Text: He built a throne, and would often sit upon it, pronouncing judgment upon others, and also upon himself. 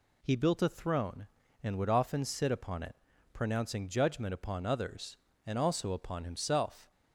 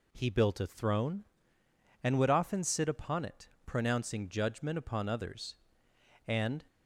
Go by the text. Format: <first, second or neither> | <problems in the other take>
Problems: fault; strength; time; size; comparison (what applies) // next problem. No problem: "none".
first | stops before "also upon himself"; at 6.6 s